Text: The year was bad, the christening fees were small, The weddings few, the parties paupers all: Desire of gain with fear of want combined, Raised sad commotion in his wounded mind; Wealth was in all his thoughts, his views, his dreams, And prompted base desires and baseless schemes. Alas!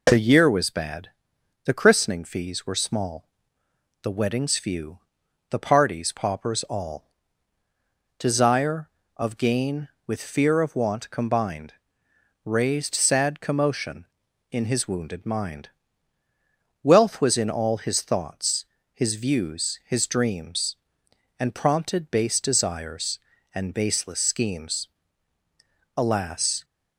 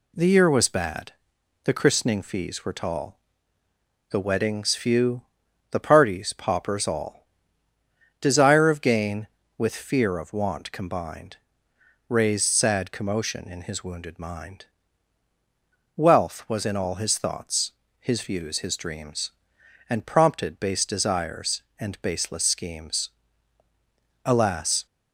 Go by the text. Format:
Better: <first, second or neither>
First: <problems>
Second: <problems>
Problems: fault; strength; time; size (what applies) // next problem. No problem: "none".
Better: first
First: none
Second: says "tall" for "small"; at 2.7 s